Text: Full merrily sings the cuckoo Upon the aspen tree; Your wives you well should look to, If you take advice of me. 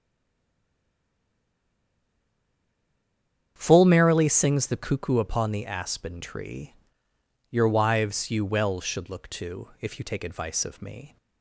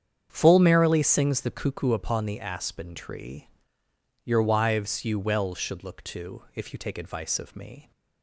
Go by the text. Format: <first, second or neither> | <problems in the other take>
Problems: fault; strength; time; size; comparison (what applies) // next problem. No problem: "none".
second | stays silent before the first word; strong; until 3.5 s; 3.5 s long // starts louder than the rest; strong; until 4.5 s; 8 dB; strong in the second